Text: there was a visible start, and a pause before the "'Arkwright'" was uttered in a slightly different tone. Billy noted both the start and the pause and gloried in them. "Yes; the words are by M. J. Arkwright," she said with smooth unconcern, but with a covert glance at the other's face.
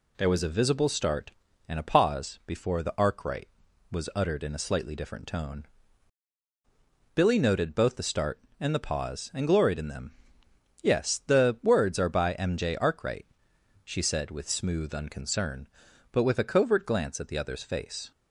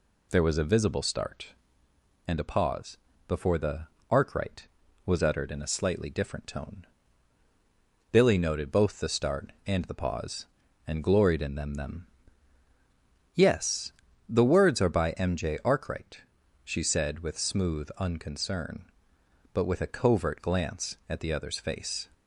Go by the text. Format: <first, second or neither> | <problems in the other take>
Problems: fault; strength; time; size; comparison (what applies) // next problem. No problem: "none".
first | pauses between "pause" and "before"; slight; at 2.9 s; 0.30 s long // pauses between "the" and "Arkwright"; slight; at 3.8 s; 0.24 s long // says "them" twice; at 11.7 s